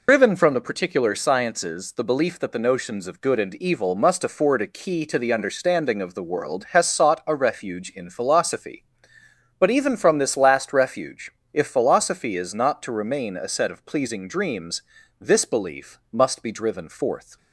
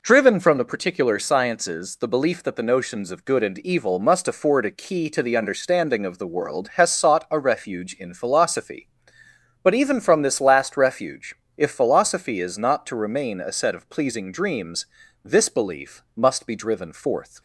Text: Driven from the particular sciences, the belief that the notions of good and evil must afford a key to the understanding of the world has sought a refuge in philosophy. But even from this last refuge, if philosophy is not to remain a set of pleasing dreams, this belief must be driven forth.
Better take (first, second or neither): second